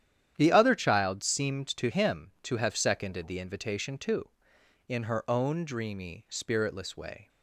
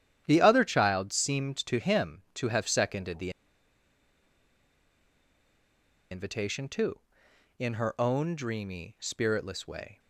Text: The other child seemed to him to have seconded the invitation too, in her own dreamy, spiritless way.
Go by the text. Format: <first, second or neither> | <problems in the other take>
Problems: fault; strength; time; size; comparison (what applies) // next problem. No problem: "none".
first | starts louder than the rest; strong; until 1.2 s; 10 dB; strong in the first // pauses between "the" and "invitation"; strong; at 3.2 s; 2.8 s long